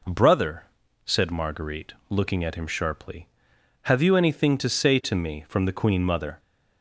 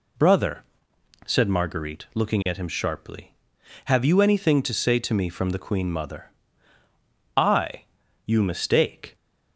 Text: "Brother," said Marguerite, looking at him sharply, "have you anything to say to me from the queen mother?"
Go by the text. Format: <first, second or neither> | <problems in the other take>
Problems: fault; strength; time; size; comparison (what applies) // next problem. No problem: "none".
first | goes on to say "I you mistake"; strong; from 7.3 s on; 1.7 s long